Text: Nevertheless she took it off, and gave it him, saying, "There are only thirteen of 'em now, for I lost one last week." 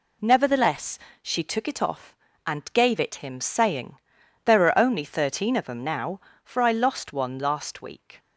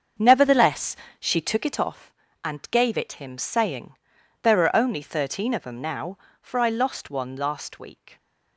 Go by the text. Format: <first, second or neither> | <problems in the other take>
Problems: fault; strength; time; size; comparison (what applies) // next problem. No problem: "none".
first | starts louder than the rest; until 1.9 s; 7 dB // pauses between "Nevertheless" and "she"; slight; at 0.9 s; 0.24 s long; slight in the first